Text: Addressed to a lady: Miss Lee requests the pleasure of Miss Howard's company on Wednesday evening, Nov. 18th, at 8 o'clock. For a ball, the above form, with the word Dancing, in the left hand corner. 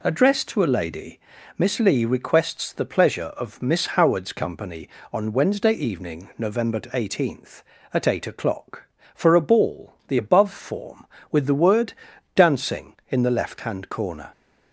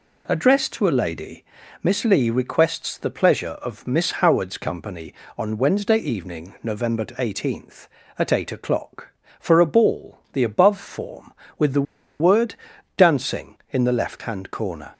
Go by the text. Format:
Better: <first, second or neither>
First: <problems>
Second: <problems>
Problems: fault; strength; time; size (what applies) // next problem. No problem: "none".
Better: first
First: pauses between "word" and "Dancing"; at 11.9 s; 0.42 s long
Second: pauses between "the" and "word"; slight; at 11.8 s; 0.35 s long // pauses between "word" and "Dancing"; at 12.5 s; 0.42 s long